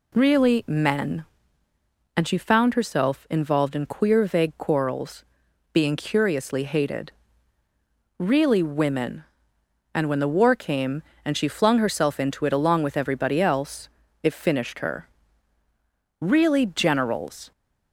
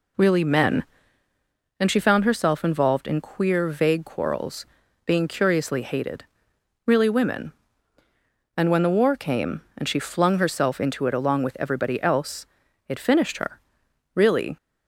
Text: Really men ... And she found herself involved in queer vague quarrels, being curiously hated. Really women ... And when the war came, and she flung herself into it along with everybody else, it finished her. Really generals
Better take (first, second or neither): first